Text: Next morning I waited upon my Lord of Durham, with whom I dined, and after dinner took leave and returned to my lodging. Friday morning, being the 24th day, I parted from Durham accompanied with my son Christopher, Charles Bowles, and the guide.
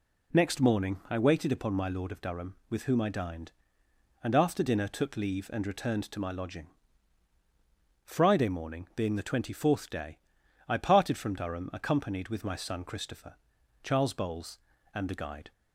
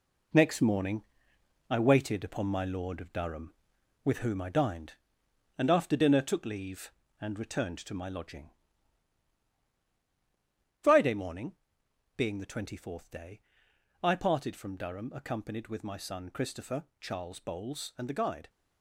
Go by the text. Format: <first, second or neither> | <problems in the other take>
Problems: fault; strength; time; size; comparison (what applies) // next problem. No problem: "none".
first | gets quieter; strong; throughout; 7.5 dB // pauses between "morning" and "I"; noticeable; at 1.0 s; 0.70 s long